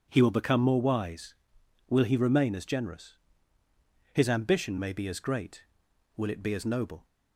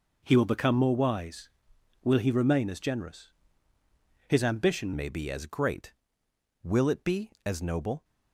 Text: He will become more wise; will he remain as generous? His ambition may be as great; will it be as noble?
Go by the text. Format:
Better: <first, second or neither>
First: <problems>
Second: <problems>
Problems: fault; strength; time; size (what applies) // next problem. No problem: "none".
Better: first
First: none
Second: changes voice at "may"; from 4.9 s on; 3.1 s long